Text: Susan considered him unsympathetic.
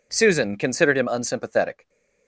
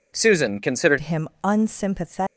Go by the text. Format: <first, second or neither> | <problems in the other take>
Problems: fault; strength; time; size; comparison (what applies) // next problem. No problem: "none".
first | changes voice at "him"; from 0.9 s on; 1.2 s long